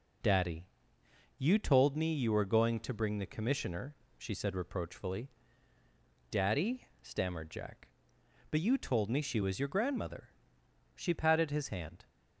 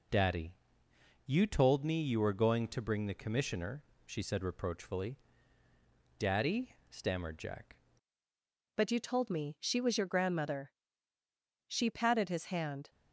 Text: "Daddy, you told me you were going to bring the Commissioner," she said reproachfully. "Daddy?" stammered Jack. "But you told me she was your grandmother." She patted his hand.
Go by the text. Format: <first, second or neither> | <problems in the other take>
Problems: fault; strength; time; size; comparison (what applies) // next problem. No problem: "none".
first | changes voice at "But"; from 8.7 s on; 4.2 s long